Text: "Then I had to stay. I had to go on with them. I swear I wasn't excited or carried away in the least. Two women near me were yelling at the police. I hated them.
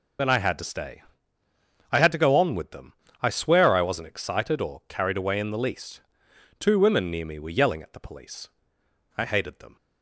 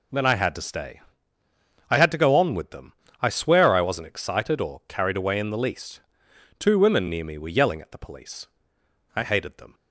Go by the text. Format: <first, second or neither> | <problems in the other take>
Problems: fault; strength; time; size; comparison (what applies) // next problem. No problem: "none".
second | loses the start of "Then"; at 0.1 s; 50 ms